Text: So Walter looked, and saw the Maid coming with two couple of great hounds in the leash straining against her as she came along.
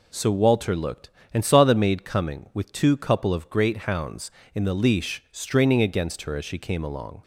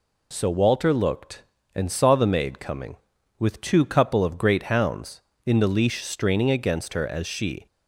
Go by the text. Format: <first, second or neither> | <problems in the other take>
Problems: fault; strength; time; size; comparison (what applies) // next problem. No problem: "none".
first | stops before "came along"; at 7.6 s